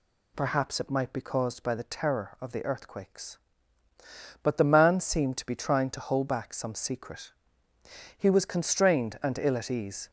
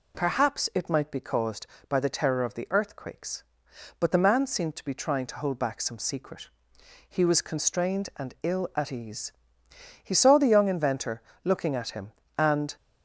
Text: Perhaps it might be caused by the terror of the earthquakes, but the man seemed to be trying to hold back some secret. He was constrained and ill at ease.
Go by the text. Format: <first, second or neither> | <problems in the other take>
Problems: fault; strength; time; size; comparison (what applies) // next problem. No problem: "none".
first | goes on to say "He saw the young inventor looking at him and"; strong; from 10.0 s on; 2.7 s long